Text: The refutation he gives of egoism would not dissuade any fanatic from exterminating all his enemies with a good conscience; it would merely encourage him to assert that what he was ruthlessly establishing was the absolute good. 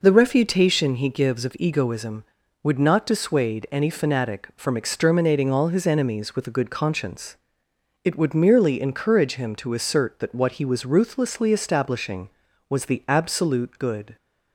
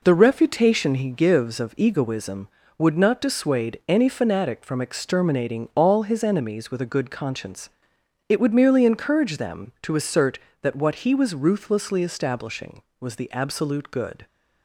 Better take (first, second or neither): first